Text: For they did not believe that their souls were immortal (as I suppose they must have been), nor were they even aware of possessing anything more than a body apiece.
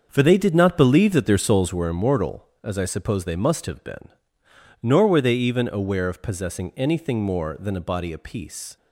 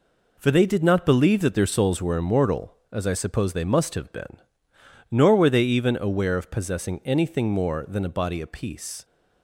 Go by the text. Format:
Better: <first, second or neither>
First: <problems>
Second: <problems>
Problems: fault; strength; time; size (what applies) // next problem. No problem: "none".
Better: second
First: starts louder than the rest; until 1.9 s; 7 dB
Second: none